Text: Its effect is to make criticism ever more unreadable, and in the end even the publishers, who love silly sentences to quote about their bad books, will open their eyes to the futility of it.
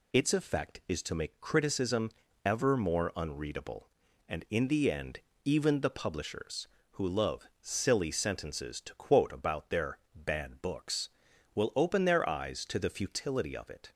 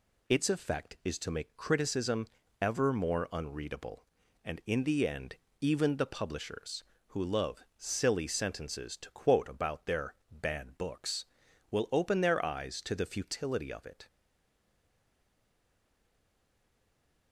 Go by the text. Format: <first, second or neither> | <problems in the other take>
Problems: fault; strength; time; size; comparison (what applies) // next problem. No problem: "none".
first | pauses between "criticism" and "ever"; slight; at 2.2 s; 0.34 s long; slight in the first // pauses between "end" and "even"; slight; at 5.3 s; 0.26 s long; slight in the first // pauses between "their" and "bad"; slight; at 10.1 s; 0.16 s long; slight in the first // stays silent after the last word; strong; from 14.0 s on; 3.3 s long